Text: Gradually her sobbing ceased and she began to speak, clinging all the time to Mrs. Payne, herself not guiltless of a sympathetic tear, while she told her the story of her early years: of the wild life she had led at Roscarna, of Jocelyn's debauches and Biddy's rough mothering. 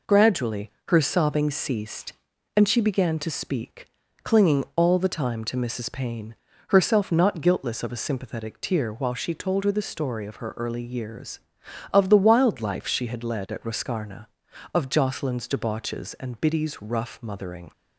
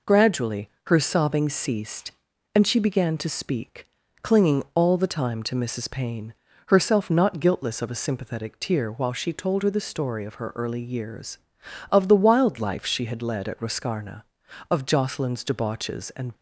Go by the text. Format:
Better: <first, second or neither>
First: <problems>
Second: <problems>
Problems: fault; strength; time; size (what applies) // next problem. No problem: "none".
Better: first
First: pauses between "Gradually" and "her"; slight; at 0.6 s; 0.20 s long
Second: pauses between "Gradually" and "her"; slight; at 0.6 s; 0.20 s long // stops before "Biddy's rough mothering"; at 16.3 s